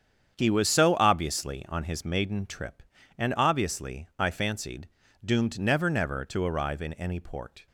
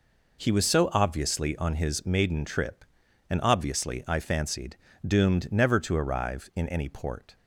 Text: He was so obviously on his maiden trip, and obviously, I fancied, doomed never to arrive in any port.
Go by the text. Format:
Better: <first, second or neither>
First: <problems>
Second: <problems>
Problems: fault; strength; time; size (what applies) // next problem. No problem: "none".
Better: second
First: starts louder than the rest; strong; until 1.3 s; 8 dB // says "never" twice; at 5.9 s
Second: none